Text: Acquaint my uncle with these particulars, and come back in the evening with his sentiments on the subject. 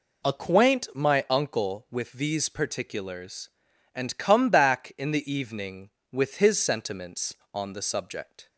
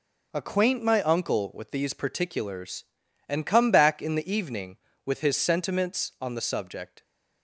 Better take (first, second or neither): neither